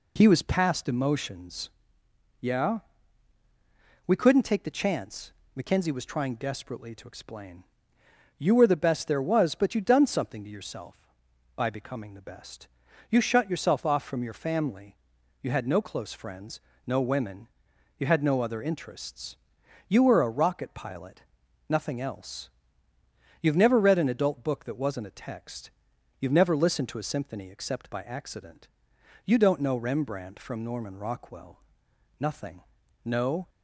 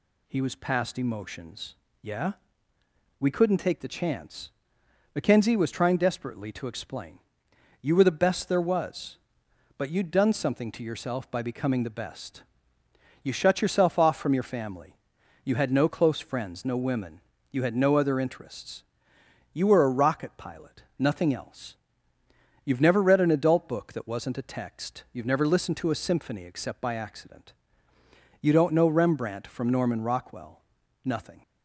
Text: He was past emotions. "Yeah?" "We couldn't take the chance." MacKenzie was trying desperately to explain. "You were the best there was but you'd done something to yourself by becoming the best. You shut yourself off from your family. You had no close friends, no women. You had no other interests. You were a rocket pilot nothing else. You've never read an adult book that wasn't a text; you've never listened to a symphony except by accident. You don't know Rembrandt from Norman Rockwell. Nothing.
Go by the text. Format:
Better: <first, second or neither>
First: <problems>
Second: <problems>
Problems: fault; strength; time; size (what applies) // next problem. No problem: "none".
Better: second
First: pauses between "pilot" and "nothing"; noticeable; at 21.2 s; 0.48 s long // goes on to say "No"; slight; from 33.0 s on; 0.46 s long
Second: none